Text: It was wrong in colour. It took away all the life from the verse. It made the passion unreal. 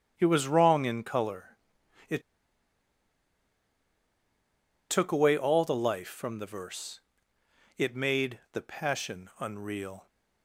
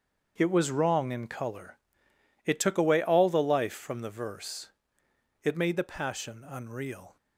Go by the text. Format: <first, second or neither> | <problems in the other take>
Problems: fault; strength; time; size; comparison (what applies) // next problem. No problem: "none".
second | starts louder than the rest; strong; until 1.1 s; 8.5 dB; also in the second // pauses between "It" and "took"; strong; at 2.2 s; 2.6 s long